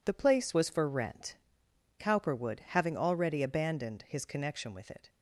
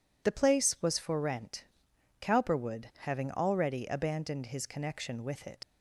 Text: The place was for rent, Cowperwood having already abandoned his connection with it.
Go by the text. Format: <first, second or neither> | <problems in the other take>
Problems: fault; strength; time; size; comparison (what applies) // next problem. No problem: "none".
first | leaves "it" unfinished; at 5.6 s; 85 ms